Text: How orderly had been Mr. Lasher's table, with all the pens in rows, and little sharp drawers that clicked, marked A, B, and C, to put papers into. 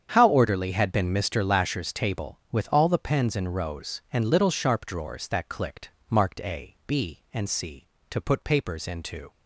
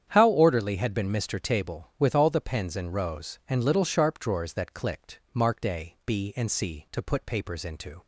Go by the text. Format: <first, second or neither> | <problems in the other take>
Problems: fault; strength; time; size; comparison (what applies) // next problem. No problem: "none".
first | starts louder than the rest; strong; until 1.1 s; 9 dB; strong in the first // skips "Lasher's"; at 1.3 s